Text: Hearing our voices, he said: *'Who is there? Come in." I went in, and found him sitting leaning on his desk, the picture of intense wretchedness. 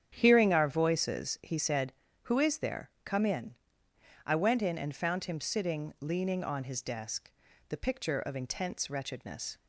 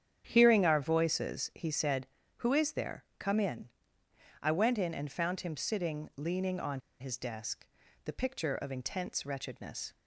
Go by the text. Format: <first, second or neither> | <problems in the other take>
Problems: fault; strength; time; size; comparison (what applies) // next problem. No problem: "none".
first | starts louder than the rest; strong; until 1.2 s; 9 dB; strong in the first // pauses between "on" and "his"; slight; at 6.7 s; 0.20 s long